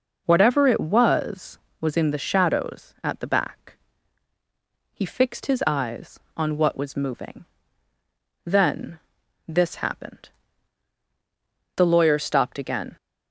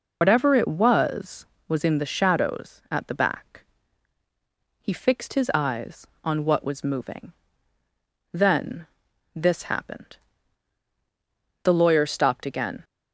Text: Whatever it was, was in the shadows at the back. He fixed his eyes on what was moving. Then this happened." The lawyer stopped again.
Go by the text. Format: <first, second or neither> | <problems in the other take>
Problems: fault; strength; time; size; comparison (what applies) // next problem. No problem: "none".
first | loses the start of "Whatever"; at 0.2 s; 75 ms // pauses between "Then" and "this"; noticeable; at 8.8 s; 0.46 s long; noticeable in the first